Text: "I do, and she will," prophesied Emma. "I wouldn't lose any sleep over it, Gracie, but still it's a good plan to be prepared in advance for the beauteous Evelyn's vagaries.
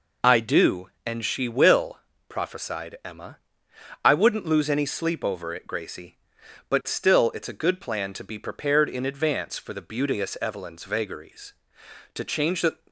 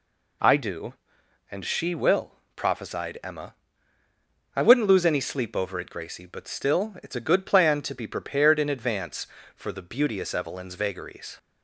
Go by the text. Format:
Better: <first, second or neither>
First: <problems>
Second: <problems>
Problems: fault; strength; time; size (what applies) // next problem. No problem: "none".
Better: second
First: goes on to say "To change the"; noticeable; from 12.1 s on; 0.62 s long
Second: none